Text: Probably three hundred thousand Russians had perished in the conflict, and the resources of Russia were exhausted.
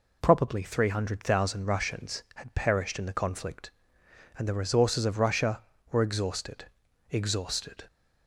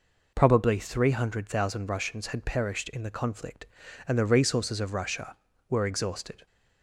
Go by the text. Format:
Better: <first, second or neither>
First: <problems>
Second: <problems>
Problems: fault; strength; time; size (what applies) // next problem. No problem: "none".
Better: second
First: says "exhausted" twice; at 7.0 s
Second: none